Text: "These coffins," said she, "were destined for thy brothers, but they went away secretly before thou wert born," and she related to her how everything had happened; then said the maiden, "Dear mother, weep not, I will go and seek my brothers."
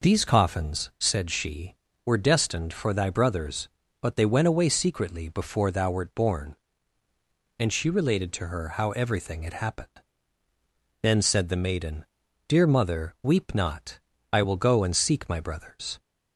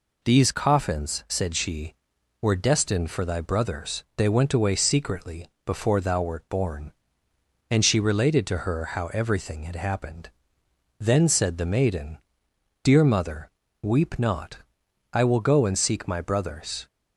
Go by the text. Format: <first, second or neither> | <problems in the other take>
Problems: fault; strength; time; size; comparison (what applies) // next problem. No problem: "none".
first | skips "but"; at 4.1 s // pauses between "secretly" and "before"; slight; at 5.4 s; 0.18 s long